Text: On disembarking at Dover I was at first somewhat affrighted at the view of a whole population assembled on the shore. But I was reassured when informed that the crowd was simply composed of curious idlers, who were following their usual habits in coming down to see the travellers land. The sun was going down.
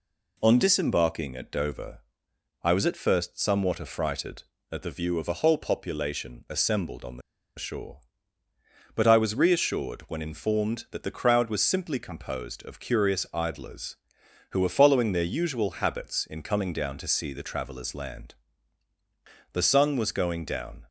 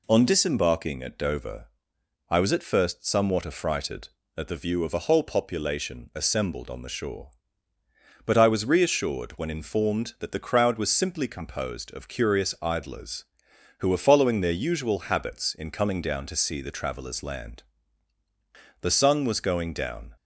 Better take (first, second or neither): second